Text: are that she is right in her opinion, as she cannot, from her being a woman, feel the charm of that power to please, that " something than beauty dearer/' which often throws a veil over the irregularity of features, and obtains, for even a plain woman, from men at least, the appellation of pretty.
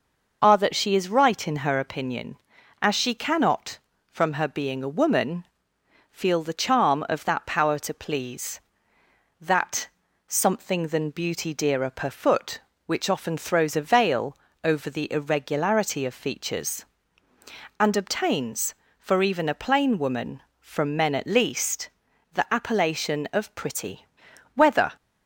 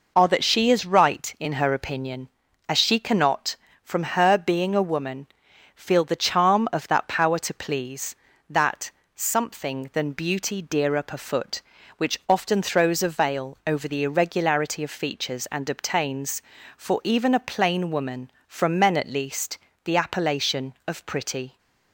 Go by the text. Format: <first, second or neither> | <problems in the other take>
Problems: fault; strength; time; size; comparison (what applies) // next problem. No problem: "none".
second | pauses between "veil" and "over"; slight; at 14.3 s; 0.28 s long // goes on to say "Whether"; slight; from 24.5 s on; 0.42 s long